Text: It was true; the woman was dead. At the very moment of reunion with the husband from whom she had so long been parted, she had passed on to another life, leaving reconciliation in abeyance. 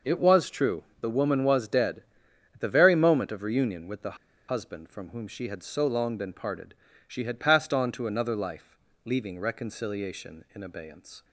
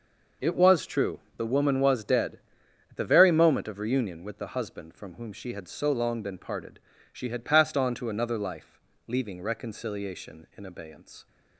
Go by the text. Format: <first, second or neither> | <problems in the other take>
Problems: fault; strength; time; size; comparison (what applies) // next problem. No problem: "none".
second | pauses between "the" and "husband"; slight; at 4.1 s; 0.31 s long